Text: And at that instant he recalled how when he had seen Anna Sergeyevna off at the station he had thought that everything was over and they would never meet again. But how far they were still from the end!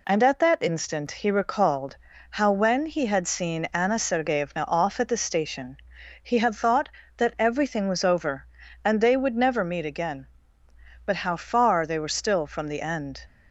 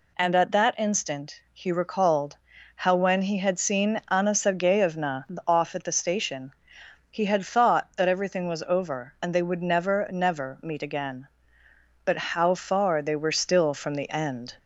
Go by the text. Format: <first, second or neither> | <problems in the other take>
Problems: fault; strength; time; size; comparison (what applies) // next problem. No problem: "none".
first | pauses between "recalled" and "how"; at 2.3 s; 0.40 s long; slight in the first // pauses between "Sergeyevna" and "off"; slight; at 5.2 s; 0.22 s long // pauses between "station" and "he"; noticeable; at 6.5 s; 0.58 s long; also in the first // says "never" twice; at 10.1 s